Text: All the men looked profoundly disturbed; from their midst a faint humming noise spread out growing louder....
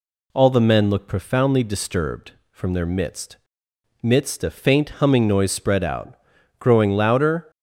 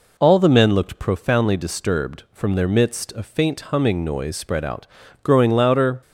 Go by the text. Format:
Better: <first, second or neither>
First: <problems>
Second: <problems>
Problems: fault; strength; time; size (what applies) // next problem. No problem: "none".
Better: second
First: says "midst" twice; at 4.0 s // pauses between "out" and "growing"; noticeable; at 6.1 s; 0.46 s long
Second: pauses between "out" and "growing"; slight; at 4.8 s; 0.34 s long